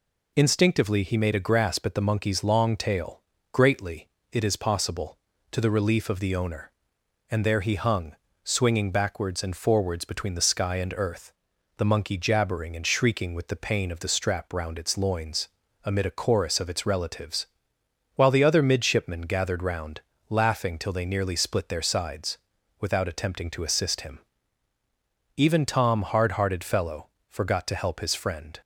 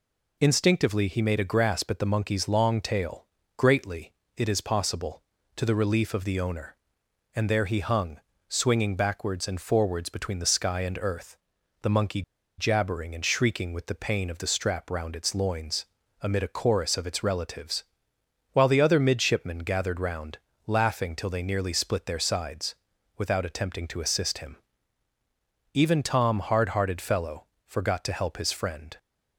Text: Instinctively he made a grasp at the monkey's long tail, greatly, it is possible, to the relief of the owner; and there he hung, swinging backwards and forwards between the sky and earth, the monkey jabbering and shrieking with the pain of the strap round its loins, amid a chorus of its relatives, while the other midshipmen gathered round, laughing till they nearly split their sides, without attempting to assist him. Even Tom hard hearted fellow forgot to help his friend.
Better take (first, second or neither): first